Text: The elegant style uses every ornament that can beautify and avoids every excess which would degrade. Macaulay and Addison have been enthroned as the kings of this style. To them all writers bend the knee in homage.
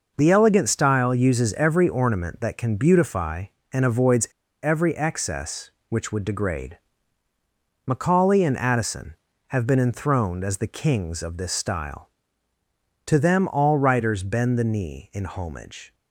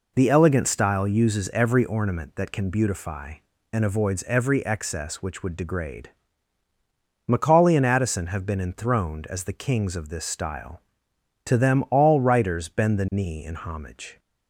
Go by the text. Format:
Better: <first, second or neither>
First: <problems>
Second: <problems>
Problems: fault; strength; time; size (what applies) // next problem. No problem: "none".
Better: second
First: pauses between "avoids" and "every"; slight; at 4.2 s; 0.34 s long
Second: none